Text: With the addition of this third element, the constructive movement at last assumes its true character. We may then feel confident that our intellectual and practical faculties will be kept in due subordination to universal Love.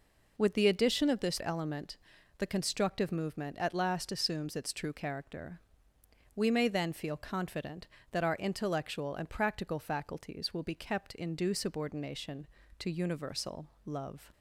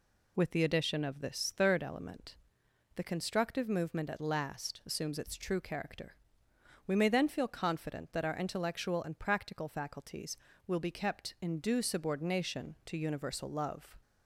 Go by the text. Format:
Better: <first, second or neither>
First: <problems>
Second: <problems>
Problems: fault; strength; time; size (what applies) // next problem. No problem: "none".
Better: second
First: skips "third"; at 1.4 s // pauses between "universal" and "Love"; slight; at 13.6 s; 0.16 s long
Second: none